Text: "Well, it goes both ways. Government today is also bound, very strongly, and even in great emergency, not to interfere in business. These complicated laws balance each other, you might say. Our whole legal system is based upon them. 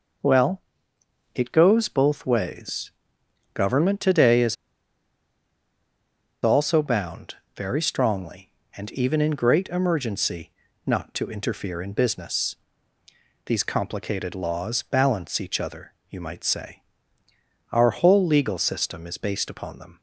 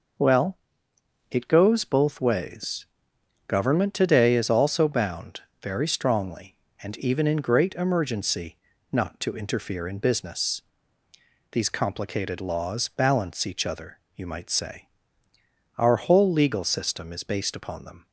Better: second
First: pauses between "is" and "also"; strong; at 4.5 s; 1.8 s long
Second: none

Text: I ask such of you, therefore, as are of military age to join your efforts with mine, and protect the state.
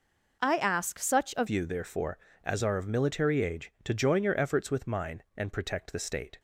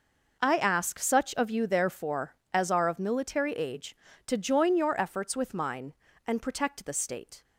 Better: second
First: changes voice at "you"; from 1.4 s on; 4.9 s long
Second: none

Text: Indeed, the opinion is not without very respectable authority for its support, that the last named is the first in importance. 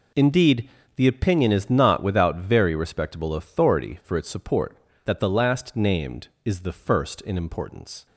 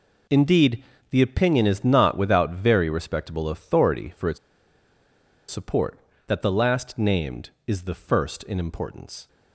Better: first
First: none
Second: pauses between "its" and "support"; at 4.3 s; 1.1 s long

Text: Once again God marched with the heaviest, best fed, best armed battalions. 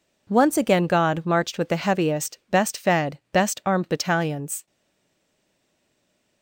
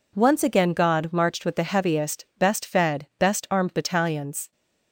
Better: second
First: stays silent after the last word; noticeable; from 4.6 s on; 1.8 s long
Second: none

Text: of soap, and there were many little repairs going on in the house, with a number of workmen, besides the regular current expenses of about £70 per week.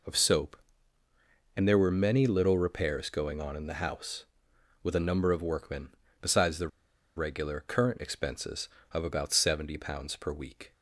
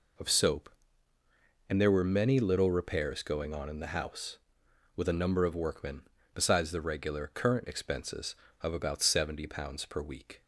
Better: second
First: pauses between "the" and "regular"; noticeable; at 6.6 s; 0.48 s long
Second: none

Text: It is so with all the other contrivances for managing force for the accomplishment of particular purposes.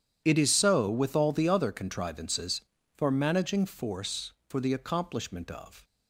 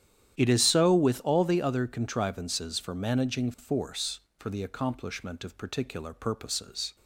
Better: second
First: starts louder than the rest; strong; until 1.2 s; 9.5 dB // stops before "particular purposes"; at 5.8 s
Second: starts louder than the rest; strong; until 1.4 s; 11 dB

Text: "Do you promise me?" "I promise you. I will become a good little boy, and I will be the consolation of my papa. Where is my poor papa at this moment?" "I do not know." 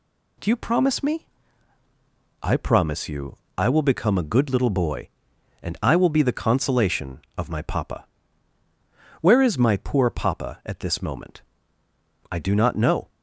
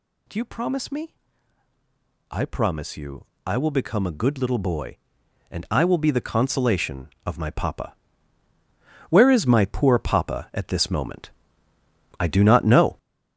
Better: first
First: none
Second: gets louder; throughout; 6.5 dB

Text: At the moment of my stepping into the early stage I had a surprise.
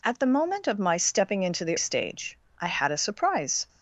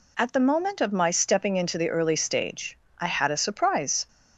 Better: second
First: skips "early"; at 1.7 s // pauses between "stage" and "I"; slight; at 2.3 s; 0.24 s long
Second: pauses between "stage" and "I"; slight; at 2.7 s; 0.24 s long

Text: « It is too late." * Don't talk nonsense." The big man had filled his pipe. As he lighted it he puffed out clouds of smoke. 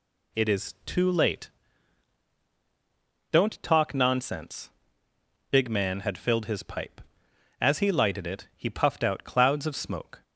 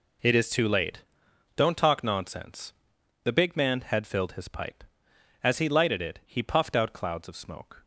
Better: second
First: skips "The"; at 5.1 s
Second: none

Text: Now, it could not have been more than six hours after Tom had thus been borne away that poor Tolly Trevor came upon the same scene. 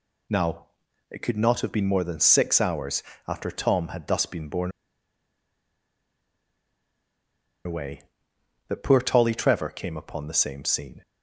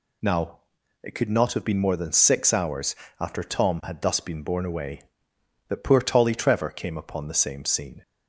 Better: second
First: pauses between "hours" and "after"; slight; at 3.0 s; 0.24 s long // pauses between "borne" and "away"; strong; at 4.7 s; 2.9 s long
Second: pauses between "hours" and "after"; slight; at 2.9 s; 0.24 s long

